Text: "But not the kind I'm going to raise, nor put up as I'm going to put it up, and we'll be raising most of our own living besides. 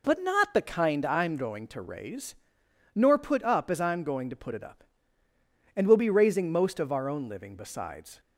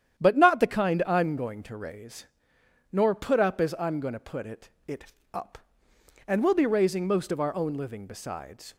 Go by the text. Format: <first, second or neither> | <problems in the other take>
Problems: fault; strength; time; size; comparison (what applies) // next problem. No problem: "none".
first | starts louder than the rest; strong; until 1.2 s; 10 dB // says "it" twice; at 4.8 s